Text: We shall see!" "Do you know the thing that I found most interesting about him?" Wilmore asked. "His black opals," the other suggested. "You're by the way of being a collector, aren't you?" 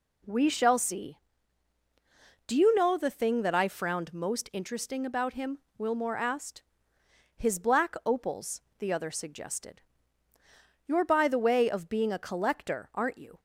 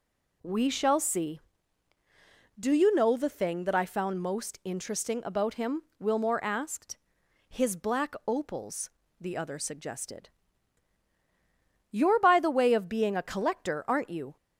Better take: second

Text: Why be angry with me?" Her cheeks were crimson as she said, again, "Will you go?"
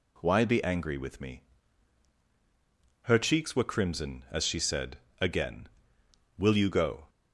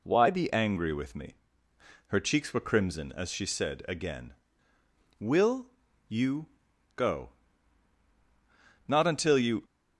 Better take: first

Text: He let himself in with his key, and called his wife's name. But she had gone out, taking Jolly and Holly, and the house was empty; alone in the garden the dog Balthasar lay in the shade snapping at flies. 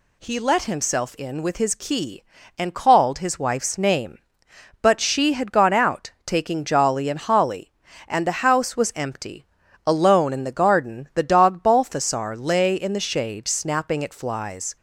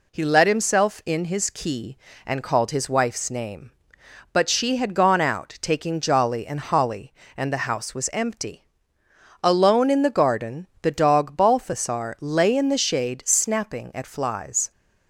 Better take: first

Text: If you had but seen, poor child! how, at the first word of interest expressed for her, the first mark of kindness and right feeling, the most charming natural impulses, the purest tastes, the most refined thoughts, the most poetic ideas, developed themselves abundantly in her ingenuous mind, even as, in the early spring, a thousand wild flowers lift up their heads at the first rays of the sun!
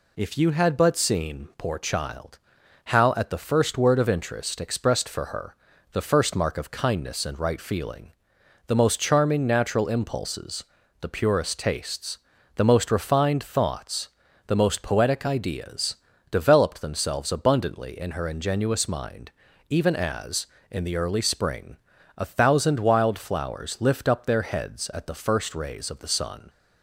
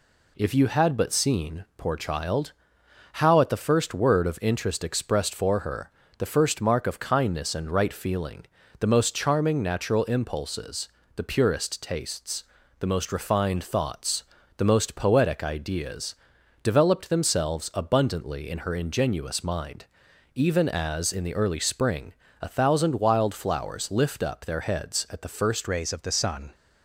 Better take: first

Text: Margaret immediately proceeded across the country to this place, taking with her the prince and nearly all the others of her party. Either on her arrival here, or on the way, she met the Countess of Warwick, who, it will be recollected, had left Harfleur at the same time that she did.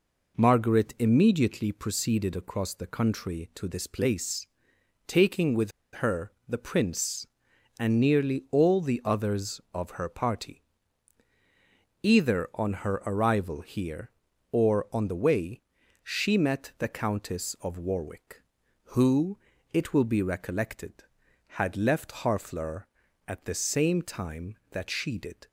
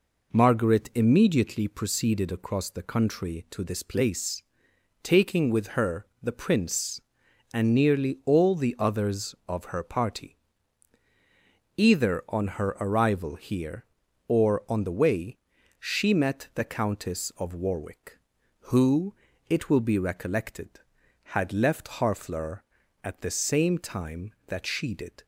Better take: second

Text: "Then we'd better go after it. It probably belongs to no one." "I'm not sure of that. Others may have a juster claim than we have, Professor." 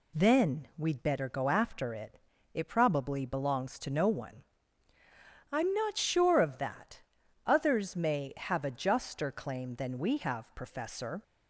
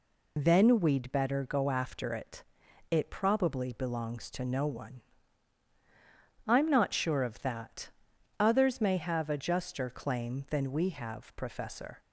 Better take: first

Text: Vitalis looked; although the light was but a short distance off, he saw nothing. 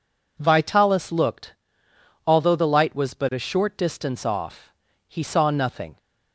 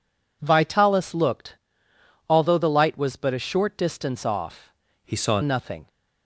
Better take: first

